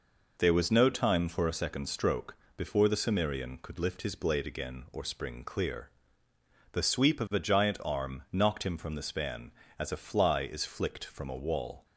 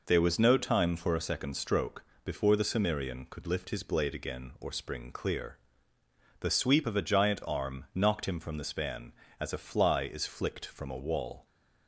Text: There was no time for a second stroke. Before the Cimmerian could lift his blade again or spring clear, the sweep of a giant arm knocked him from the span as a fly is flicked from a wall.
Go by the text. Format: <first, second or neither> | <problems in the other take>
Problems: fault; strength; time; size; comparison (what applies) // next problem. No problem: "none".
neither | none